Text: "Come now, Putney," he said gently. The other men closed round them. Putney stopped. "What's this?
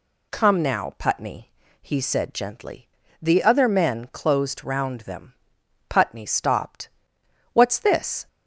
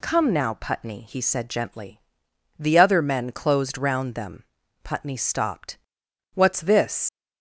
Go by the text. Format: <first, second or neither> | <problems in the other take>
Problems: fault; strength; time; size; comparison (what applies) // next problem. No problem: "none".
first | leaves "this" unfinished; at 7.0 s; 105 ms